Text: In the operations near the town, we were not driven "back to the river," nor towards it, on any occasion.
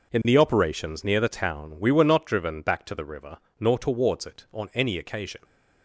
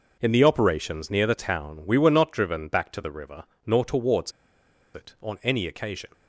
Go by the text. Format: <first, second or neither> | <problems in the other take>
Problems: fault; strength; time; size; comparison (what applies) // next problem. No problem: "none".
first | pauses between "towards" and "it"; noticeable; at 4.3 s; 0.63 s long